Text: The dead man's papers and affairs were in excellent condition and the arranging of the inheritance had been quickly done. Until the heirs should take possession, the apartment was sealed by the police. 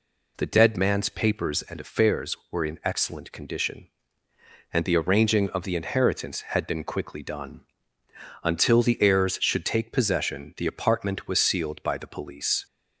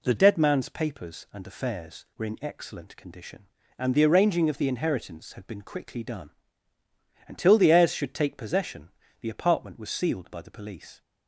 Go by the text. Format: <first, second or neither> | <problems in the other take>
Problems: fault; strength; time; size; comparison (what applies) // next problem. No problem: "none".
first | changes voice at "dead"; from 0.1 s on; 10.9 s long